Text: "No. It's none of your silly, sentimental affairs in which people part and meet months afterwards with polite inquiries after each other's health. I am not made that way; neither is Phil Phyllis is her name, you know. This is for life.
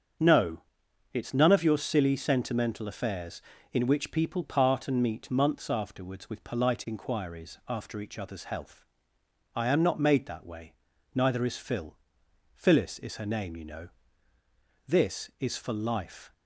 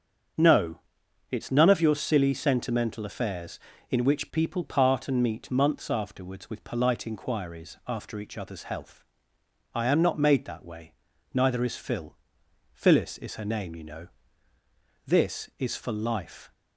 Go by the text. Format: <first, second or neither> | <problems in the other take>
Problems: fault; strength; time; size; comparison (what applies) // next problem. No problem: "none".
neither | starts louder than the rest; strong; the same in both // pauses between "Phil" and "Phyllis"; noticeable; the same in both